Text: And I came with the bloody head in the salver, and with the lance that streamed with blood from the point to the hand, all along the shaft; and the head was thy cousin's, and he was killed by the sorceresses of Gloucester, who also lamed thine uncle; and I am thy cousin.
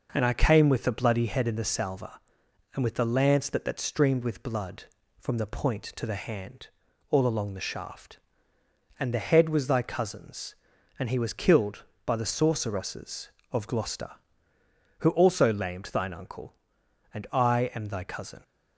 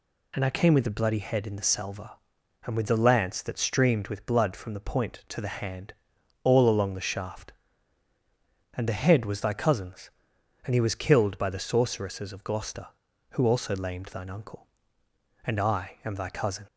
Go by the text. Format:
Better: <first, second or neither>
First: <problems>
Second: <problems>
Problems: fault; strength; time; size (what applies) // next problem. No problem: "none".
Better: second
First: says "that" twice; at 3.6 s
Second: none